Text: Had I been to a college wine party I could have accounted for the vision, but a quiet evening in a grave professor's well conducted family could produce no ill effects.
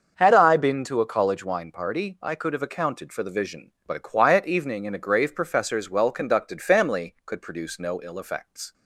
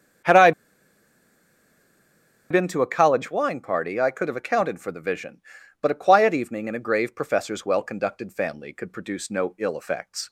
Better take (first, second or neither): first